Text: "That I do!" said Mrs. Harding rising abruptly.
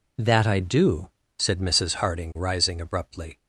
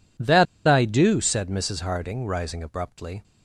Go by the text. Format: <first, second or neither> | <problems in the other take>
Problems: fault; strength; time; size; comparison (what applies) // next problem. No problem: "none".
first | pauses between "That" and "I"; slight; at 0.4 s; 0.21 s long